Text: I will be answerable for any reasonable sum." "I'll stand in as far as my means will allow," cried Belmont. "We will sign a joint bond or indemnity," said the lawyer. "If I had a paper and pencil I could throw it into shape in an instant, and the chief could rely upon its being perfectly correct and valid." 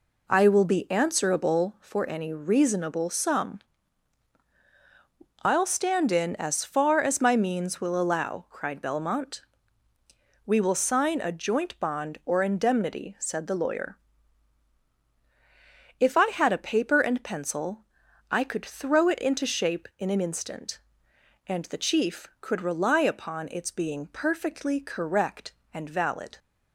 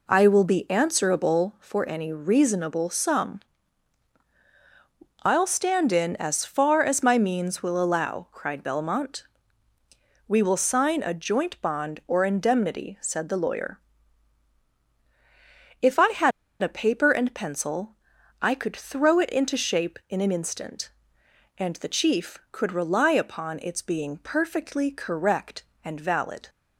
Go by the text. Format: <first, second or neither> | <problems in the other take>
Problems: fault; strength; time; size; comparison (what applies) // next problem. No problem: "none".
first | pauses between "had" and "a"; slight; at 16.3 s; 0.31 s long // pauses between "pencil" and "I"; noticeable; at 17.9 s; 0.46 s long; noticeable in the first